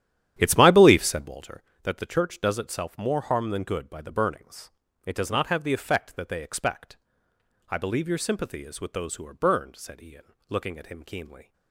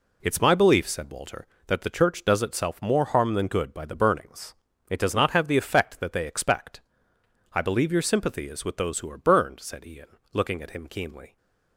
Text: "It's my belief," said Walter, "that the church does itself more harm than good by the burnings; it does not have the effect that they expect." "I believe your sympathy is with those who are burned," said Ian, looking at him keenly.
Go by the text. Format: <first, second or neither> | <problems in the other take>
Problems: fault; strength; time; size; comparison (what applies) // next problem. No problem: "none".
second | starts louder than the rest; strong; until 1.4 s; 11 dB